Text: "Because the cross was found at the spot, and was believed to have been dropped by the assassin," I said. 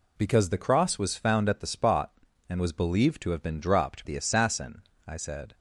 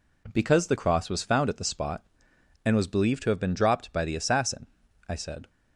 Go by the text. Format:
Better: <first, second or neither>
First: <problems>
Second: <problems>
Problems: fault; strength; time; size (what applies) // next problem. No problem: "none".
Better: second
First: skips "by"; at 4.0 s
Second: none